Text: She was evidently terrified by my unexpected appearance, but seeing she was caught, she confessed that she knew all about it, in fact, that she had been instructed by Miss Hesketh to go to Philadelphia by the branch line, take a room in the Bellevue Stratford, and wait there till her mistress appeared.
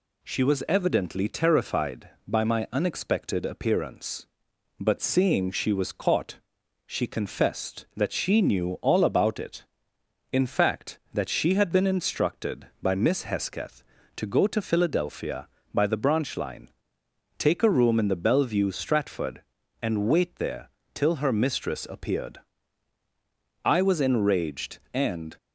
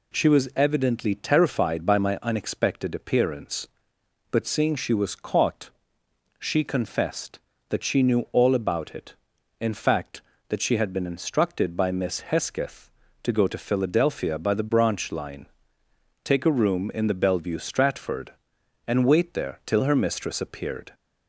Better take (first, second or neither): second